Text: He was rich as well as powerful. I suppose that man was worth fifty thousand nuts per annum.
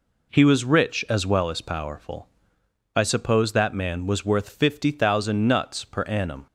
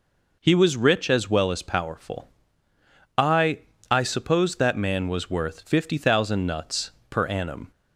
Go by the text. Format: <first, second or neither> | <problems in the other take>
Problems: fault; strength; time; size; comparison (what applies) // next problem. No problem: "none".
first | says "I" twice; at 3.9 s // pauses between "nuts" and "per"; slight; at 6.9 s; 0.20 s long